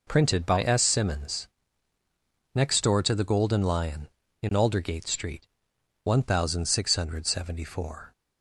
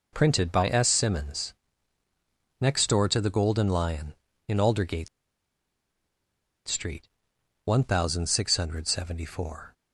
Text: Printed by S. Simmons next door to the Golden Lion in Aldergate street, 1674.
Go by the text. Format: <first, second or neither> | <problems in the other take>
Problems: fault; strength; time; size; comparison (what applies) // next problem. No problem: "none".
first | pauses between "Simmons" and "next"; at 1.5 s; 1.0 s long; also in the first // pauses between "Aldergate" and "street"; strong; at 5.0 s; 1.5 s long